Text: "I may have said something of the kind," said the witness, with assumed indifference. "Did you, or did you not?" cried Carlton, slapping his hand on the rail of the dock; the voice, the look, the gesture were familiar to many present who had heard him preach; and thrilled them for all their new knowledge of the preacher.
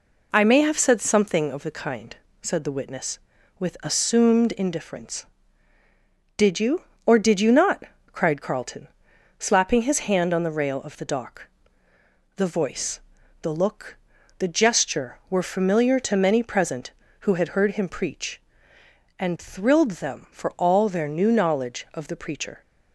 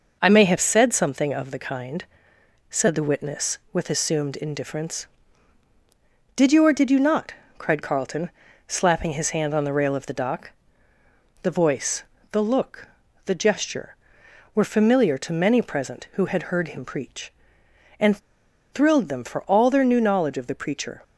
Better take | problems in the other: first | pauses between "and" and "thrilled"; noticeable; at 18.1 s; 0.53 s long

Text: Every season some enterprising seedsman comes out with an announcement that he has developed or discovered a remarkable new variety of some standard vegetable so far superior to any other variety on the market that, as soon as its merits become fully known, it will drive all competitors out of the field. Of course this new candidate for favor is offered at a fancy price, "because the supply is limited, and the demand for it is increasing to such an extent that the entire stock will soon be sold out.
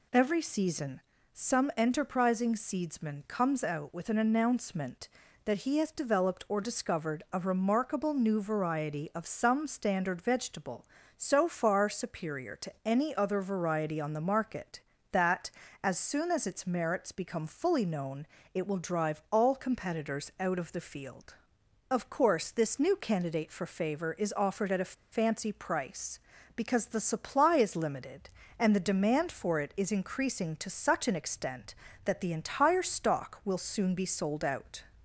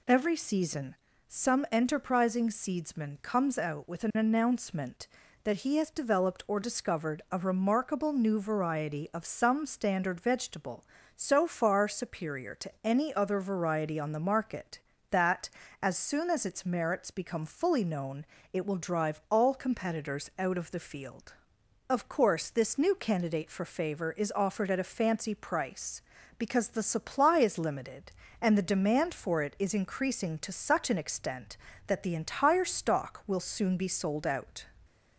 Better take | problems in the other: second | pauses between "season" and "some"; slight; at 1.0 s; 0.34 s long; slight in the second // pauses between "a" and "fancy"; slight; at 24.9 s; 0.19 s long

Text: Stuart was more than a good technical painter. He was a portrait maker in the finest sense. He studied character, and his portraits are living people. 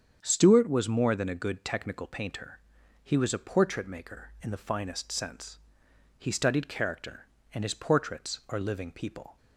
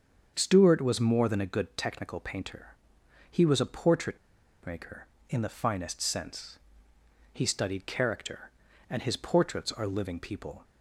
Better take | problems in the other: first | starts louder than the rest; until 1.3 s; 7 dB; strong in the first // pauses between "portrait" and "maker"; noticeable; at 4.1 s; 0.47 s long

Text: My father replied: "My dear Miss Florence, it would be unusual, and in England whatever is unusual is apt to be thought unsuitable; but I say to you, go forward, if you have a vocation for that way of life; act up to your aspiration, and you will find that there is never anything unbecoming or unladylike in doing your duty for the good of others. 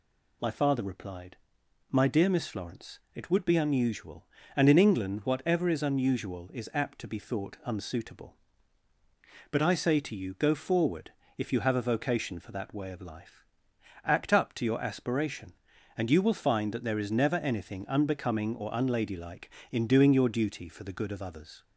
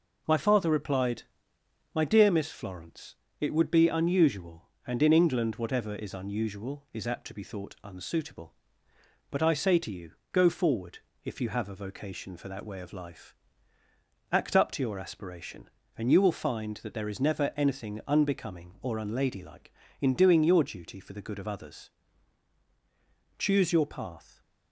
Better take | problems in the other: first | goes on to say "Choose your path"; noticeable; from 23.3 s on; 1.0 s long

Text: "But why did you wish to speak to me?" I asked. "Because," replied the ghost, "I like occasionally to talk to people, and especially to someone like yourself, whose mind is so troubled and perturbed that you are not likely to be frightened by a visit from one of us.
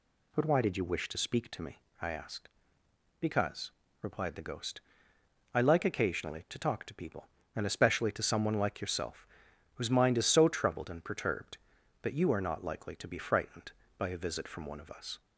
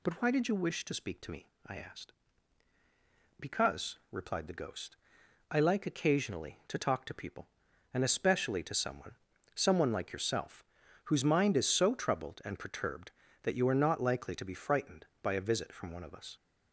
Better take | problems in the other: first | says "someone" twice; at 9.5 s

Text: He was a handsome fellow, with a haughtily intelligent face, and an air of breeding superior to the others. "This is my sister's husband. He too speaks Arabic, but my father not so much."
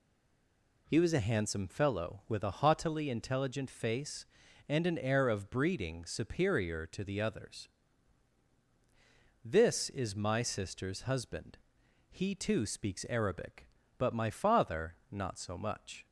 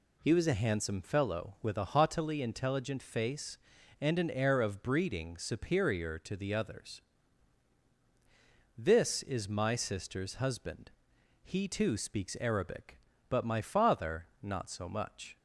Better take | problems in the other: second | stays silent before the first word; slight; until 0.8 s; 0.8 s long

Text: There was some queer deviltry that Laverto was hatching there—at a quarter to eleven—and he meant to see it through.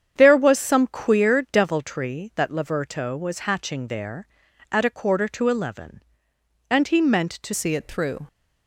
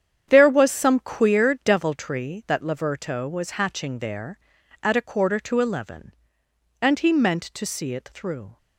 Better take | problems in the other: second | starts louder than the rest; strong; until 1.1 s; 8.5 dB; strong in the second // changes voice at "see"; from 7.5 s on; 0.7 s long

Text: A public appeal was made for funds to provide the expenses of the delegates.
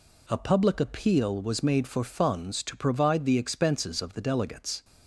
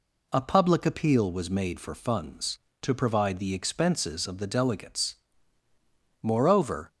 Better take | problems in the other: first | goes on to say "Moreover"; noticeable; from 6.2 s on; 0.70 s long

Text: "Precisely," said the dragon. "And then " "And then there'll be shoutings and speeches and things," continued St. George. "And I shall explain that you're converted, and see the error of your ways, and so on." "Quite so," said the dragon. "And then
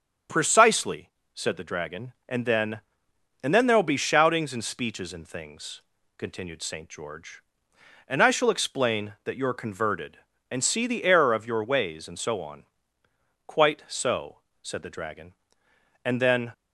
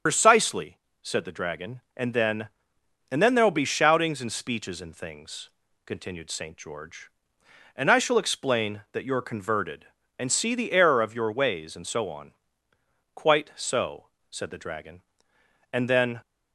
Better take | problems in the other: first | loses the start of "Precisely"; at 0.0 s; 75 ms

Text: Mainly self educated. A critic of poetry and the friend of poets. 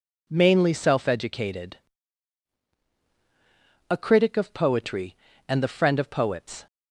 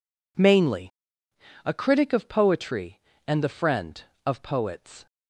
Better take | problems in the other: first | skips "self educated"; at 1.2 s

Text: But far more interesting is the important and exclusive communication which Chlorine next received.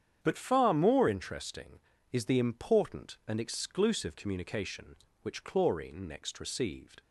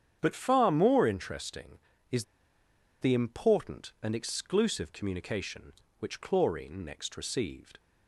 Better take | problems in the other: first | starts louder than the rest; strong; until 1.2 s; 9 dB; strong in the first // pauses between "is" and "the"; noticeable; at 2.2 s; 0.77 s long

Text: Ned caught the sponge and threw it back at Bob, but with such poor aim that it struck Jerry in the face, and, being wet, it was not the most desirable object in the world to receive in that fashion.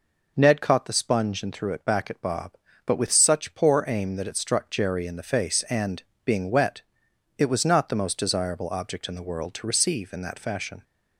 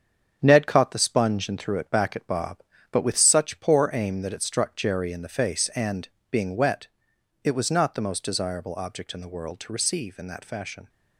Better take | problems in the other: first | gets quieter; throughout; 6.5 dB

